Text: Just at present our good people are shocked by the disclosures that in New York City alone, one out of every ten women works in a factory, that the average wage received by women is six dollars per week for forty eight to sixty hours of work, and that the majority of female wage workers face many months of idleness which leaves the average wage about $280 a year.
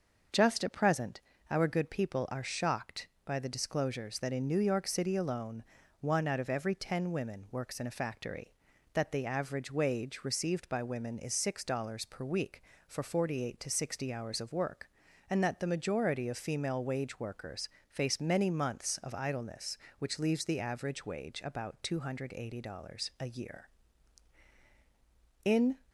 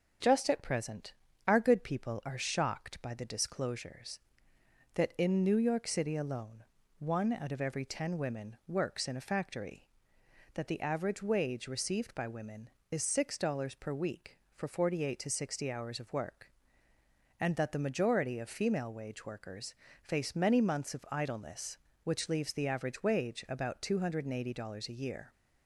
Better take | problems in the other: second | starts louder than the rest; until 1.6 s; 6.5 dB; also in the second // pauses between "present" and "our"; slight; at 1.2 s; 0.28 s long; slight in the second // pauses between "workers" and "face"; slight; at 17.6 s; 0.20 s long; slight in the second // goes on to say "In"; slight; from 25.4 s on; 0.32 s long

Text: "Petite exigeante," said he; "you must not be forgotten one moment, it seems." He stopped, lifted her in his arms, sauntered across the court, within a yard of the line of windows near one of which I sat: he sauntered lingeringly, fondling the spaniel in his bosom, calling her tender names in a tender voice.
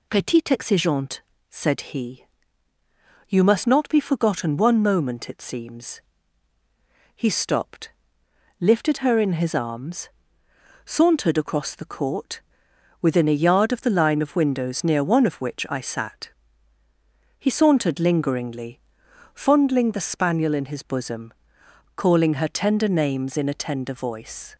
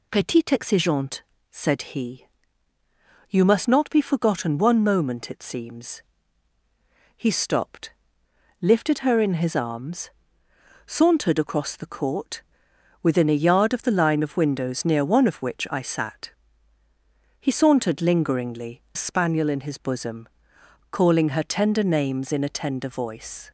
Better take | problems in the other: first | skips "fondling the"; at 18.8 s

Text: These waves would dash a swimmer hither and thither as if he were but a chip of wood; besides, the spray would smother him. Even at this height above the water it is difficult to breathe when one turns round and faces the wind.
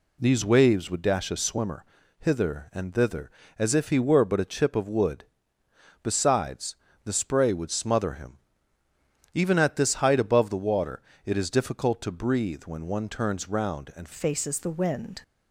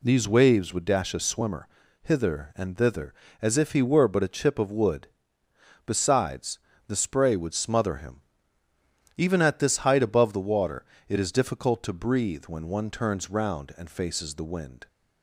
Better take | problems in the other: second | pauses between "swimmer" and "hither"; at 1.8 s; 0.38 s long; also in the second // pauses between "water" and "it"; slight; at 11.0 s; 0.22 s long; slight in the second // changes voice at "faces"; from 14.1 s on; 1.1 s long

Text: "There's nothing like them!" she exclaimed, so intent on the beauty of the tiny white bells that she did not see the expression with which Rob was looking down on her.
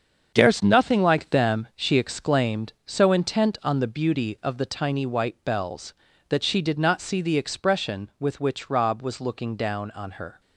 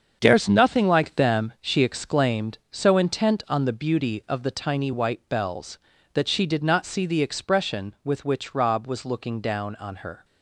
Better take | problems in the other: neither | starts louder than the rest; the same in both

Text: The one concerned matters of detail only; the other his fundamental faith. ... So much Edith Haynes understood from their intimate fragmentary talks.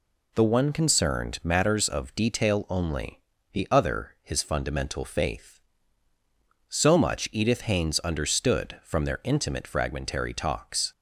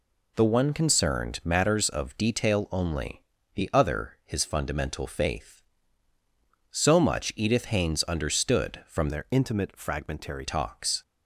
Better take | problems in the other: first | changes voice from "their" to "fragmentary"; from 9.0 to 10.4 s; 1.4 s long

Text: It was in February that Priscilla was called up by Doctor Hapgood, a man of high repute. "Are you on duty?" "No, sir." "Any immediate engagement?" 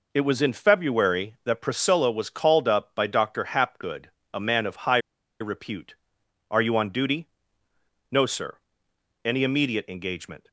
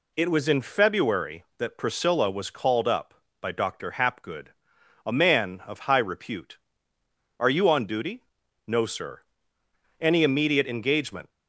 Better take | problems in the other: second | pauses between "high" and "repute"; at 4.9 s; 0.42 s long

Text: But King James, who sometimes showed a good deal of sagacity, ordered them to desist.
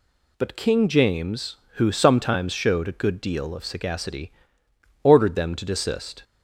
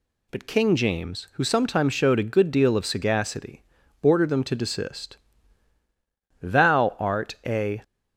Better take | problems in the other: first | goes on to say "Thou art a"; from 6.4 s on; 1.4 s long

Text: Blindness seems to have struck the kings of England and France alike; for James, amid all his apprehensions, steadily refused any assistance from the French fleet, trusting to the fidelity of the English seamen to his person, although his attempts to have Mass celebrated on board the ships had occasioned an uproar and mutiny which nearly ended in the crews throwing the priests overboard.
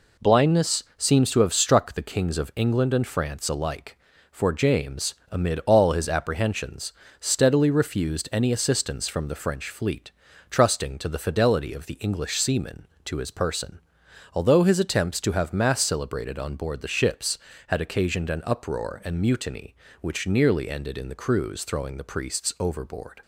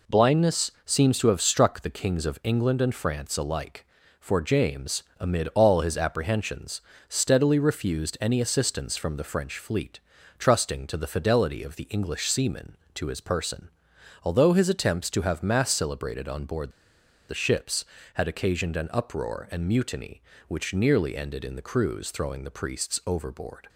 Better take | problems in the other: first | pauses between "board" and "the"; noticeable; at 16.6 s; 0.59 s long

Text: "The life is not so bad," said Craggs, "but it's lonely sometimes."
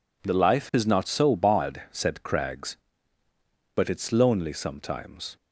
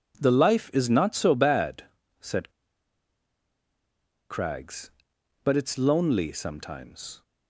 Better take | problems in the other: first | pauses between "said" and "Craggs"; strong; at 2.4 s; 1.8 s long

